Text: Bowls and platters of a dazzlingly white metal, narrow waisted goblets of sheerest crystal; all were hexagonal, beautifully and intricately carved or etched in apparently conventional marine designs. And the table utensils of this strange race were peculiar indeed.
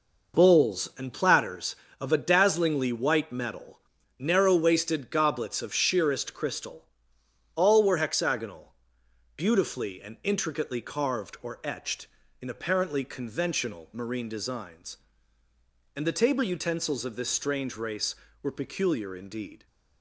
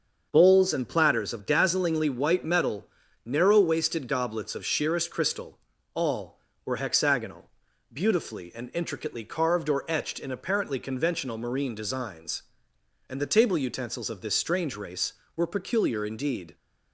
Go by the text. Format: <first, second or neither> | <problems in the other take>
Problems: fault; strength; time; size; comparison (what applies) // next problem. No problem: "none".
first | starts louder than the rest; until 1.3 s; 6.5 dB // skips "a"; at 1.3 s